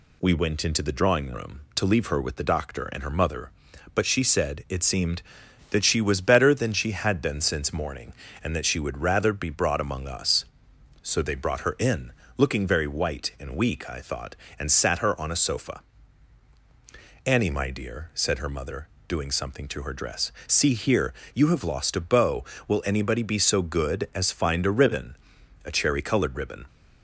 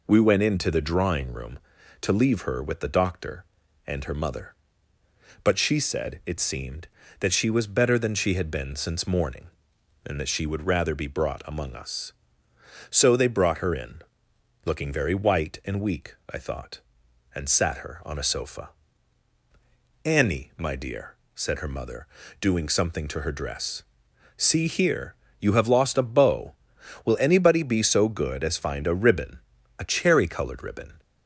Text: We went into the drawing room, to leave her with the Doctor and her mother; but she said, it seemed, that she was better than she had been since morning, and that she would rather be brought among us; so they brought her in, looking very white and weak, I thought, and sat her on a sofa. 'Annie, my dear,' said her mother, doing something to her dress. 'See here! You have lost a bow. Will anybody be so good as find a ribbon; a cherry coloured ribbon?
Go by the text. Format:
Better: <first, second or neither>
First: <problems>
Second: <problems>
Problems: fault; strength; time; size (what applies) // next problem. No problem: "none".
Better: neither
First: none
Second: none